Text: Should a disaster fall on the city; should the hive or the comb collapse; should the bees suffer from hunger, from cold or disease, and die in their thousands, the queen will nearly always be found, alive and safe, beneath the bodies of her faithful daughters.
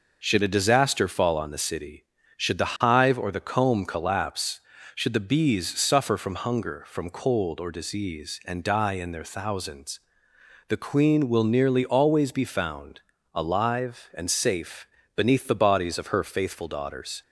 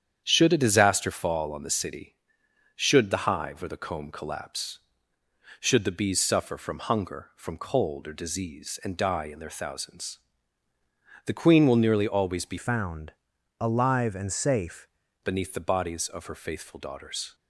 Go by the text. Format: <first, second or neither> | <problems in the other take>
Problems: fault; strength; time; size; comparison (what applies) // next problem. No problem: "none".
first | starts louder than the rest; strong; until 1.2 s; 9 dB // changes voice from "found" to "safe"; from 12.5 to 14.8 s; 2.3 s long